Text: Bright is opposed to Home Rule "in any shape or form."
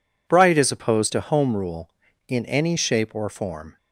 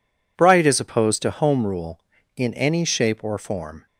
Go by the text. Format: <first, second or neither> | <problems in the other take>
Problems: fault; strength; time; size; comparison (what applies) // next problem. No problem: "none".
neither | none